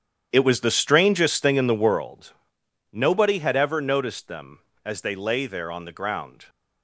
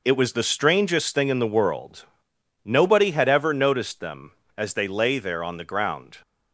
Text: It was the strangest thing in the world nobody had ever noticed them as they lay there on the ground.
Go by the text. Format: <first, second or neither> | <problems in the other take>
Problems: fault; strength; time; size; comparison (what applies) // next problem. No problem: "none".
second | starts louder than the rest; strong; until 2.0 s; 9.5 dB // pauses between "world" and "nobody"; noticeable; at 2.3 s; 0.62 s long; noticeable in the second